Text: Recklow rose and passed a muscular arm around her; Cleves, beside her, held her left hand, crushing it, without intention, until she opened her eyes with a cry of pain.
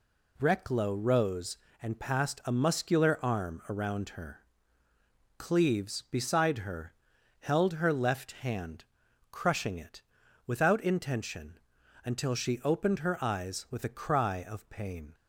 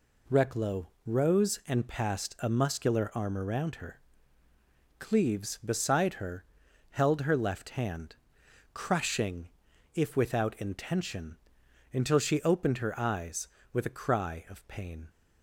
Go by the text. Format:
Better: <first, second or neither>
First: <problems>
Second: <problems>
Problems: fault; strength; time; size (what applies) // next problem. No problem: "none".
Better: first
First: none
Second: pauses between "Recklow" and "rose"; slight; at 0.8 s; 0.18 s long // says "if" for "it"; at 9.9 s